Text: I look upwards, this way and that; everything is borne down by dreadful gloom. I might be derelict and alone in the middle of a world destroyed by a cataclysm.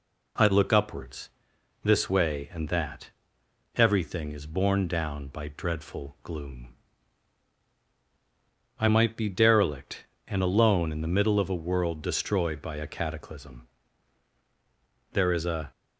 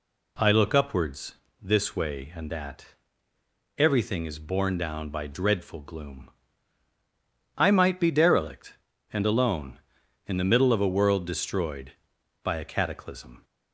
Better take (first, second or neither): second